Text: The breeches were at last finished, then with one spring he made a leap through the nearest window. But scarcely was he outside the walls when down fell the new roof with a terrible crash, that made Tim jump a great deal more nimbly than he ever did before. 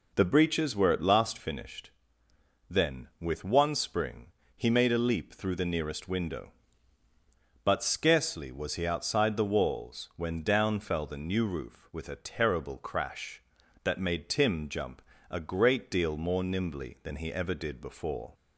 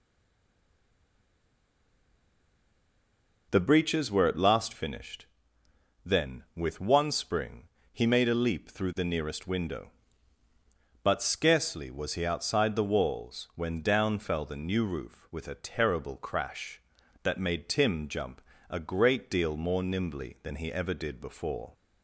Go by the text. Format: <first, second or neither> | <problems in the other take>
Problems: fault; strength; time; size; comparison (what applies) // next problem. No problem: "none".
first | stays silent before the first word; strong; until 3.5 s; 3.5 s long // pauses between "spring" and "he"; slight; at 7.6 s; 0.24 s long; slight in the first // pauses between "jump" and "a"; slight; at 18.3 s; 0.30 s long; slight in the first